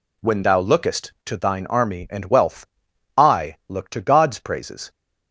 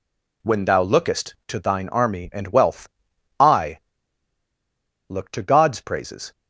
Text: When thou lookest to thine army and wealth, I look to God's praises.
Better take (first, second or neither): first